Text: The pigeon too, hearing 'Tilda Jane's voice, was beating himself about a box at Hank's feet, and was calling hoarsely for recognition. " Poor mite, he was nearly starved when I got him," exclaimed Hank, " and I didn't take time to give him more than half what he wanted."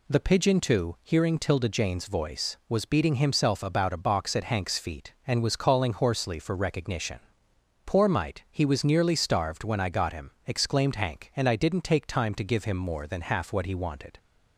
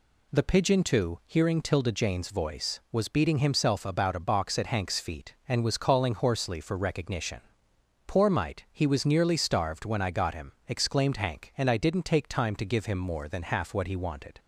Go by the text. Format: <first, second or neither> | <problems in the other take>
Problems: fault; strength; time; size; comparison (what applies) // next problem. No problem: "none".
neither | none